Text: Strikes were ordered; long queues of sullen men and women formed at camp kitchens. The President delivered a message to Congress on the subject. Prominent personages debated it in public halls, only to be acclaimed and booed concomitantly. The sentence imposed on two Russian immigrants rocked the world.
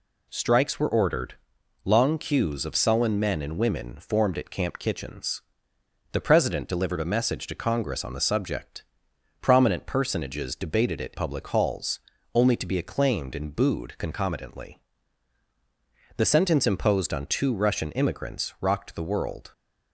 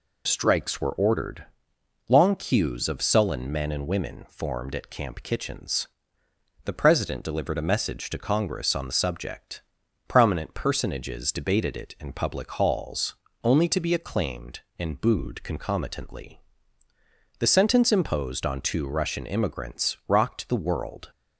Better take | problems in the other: second | skips "in"; at 11.1 s

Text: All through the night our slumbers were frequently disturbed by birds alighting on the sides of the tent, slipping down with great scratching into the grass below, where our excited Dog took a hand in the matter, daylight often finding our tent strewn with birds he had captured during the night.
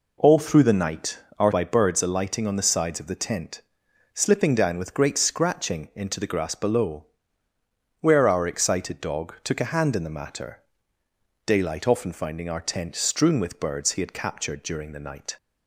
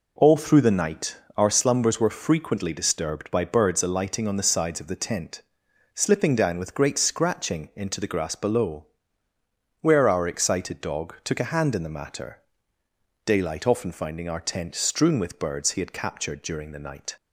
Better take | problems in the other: second | pauses between "night" and "our"; slight; at 1.1 s; 0.20 s long; slight in the second // skips "slumbers were frequently disturbed"; at 1.5 s

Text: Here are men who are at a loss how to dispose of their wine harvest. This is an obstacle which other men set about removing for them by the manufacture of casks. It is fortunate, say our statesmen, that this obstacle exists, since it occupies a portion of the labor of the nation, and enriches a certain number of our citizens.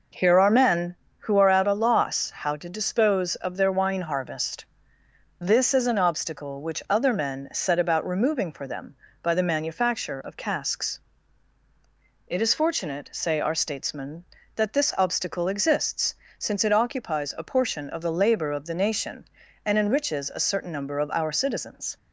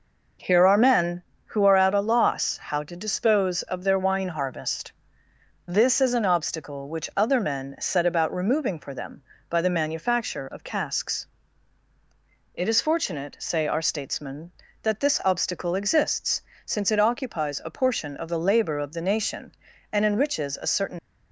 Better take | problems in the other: first | stops before "number of our citizens"; at 20.9 s

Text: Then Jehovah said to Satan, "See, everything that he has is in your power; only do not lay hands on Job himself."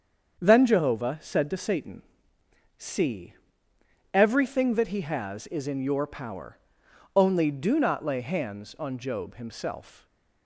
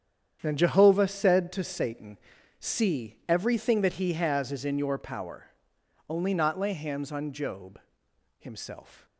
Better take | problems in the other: first | starts louder than the rest; strong; until 1.4 s; 8.5 dB; strong in the first // skips "do"; at 6.3 s // pauses between "Job" and "himself"; noticeable; at 7.7 s; 0.58 s long

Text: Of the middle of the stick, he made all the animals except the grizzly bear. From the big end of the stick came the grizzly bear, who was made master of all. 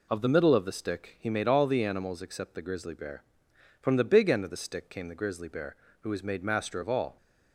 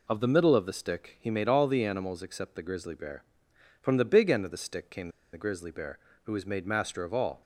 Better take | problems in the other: first | pauses between "came" and "the"; slight; at 5.0 s; 0.24 s long

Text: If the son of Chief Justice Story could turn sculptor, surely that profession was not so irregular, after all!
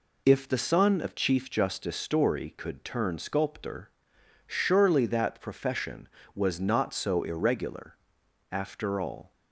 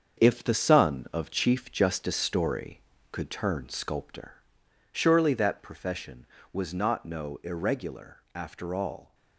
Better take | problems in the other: first | starts louder than the rest; until 1.2 s; 7 dB // says "no" for "so"; at 7.0 s

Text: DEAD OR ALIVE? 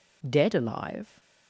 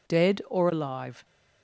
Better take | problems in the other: second | skips "OR"; at 0.5 s

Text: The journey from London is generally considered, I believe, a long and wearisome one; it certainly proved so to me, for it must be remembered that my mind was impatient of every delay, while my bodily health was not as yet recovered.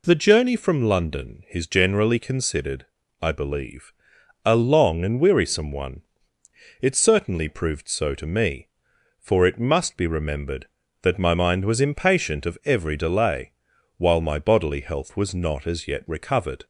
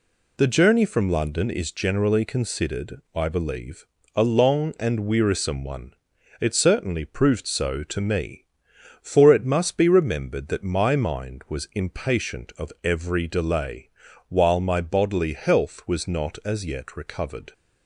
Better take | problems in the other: neither | none

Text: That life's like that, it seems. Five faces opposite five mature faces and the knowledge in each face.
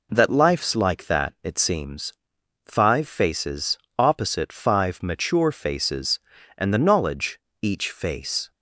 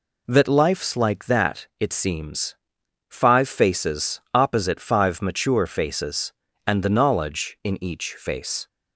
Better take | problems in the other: second | pauses between "faces" and "opposite"; slight; at 3.7 s; 0.18 s long // skips "in"; at 7.4 s

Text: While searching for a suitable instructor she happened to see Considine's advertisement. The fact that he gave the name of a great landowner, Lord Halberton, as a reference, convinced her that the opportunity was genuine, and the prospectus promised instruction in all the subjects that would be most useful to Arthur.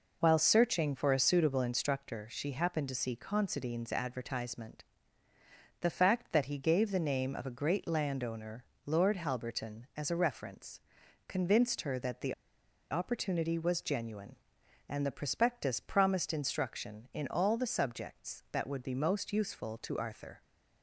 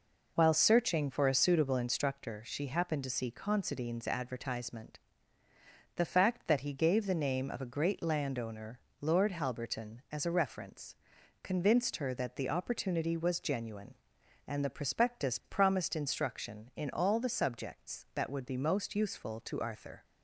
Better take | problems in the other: second | pauses between "the" and "opportunity"; noticeable; at 12.3 s; 0.57 s long

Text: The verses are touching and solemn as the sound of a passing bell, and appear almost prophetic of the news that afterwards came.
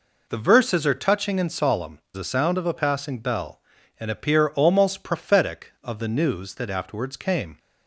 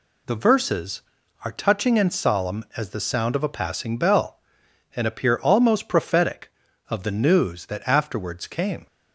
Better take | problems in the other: second | skips "as"; at 2.0 s

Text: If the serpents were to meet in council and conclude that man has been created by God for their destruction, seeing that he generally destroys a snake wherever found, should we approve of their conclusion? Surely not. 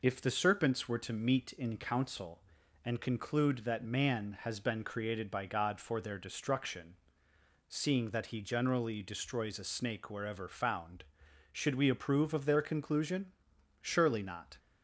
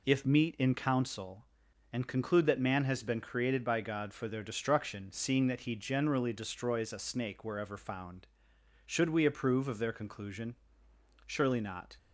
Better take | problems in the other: first | skips "the serpents were to"; at 0.2 s

